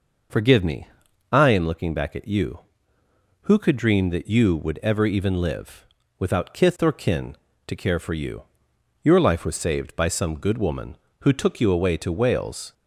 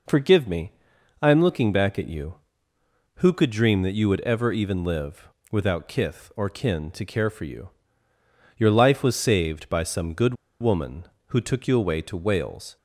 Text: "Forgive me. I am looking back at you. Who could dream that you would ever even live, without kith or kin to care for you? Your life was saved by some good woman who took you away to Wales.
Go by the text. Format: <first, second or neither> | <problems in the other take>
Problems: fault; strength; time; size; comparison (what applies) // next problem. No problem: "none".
first | pauses between "good" and "woman"; slight; at 10.3 s; 0.26 s long